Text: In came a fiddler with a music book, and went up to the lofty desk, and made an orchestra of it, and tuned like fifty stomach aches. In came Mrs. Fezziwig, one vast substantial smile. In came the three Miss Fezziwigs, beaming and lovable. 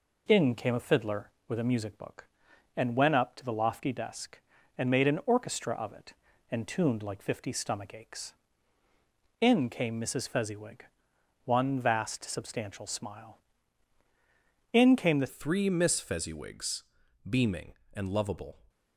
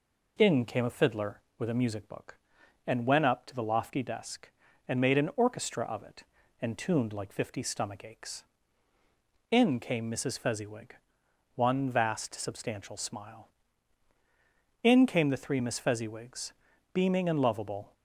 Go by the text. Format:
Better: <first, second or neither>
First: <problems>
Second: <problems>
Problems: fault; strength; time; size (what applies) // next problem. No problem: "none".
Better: second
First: changes voice at "three"; from 15.2 s on; 3.3 s long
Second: none